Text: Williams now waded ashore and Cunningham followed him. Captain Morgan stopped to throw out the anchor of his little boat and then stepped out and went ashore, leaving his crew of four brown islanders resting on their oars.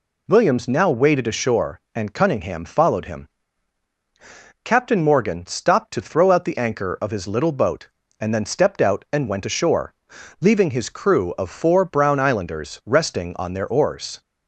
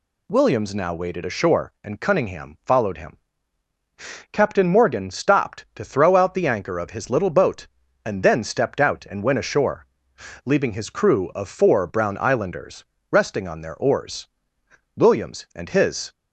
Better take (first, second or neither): first